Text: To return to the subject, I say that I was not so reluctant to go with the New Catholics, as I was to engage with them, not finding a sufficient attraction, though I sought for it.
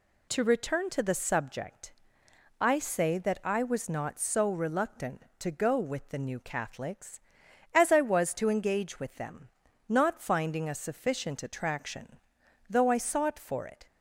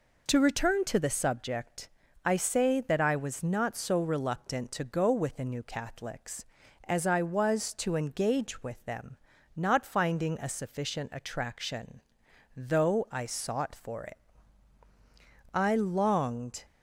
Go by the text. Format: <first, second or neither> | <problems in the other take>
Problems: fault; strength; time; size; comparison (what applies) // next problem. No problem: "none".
first | goes on to say "I longed"; noticeable; from 15.5 s on; 1.1 s long